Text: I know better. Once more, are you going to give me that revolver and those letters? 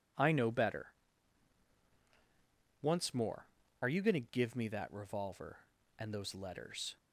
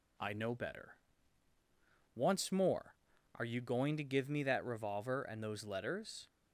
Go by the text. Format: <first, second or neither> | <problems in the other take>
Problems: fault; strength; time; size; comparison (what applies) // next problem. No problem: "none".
neither | none